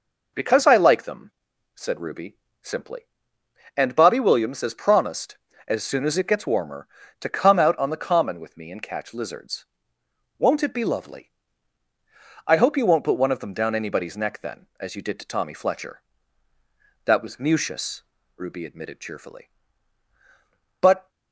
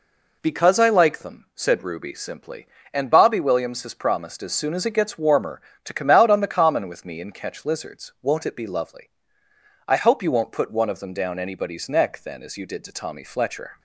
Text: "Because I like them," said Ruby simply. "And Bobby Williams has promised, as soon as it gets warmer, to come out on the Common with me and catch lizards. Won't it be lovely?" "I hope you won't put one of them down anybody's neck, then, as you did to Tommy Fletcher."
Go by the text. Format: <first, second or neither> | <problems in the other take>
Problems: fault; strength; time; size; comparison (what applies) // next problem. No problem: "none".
second | pauses between "Ruby" and "simply"; slight; at 2.3 s; 0.24 s long // goes on to say "That was Mucius Ruby admitted cheerfully But"; strong; from 17.0 s on; 4.0 s long